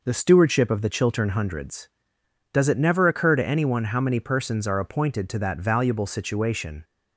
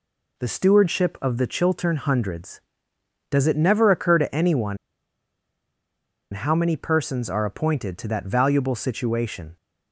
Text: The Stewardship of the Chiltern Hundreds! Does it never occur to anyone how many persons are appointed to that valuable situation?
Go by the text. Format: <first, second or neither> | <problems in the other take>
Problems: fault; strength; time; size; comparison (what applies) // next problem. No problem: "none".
first | pauses between "anyone" and "how"; strong; at 4.7 s; 1.5 s long